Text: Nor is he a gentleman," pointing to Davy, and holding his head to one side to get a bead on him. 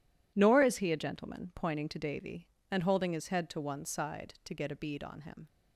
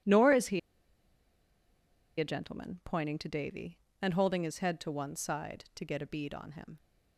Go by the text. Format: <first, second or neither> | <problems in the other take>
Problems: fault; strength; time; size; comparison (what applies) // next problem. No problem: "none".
first | pauses between "he" and "a"; strong; at 0.5 s; 1.5 s long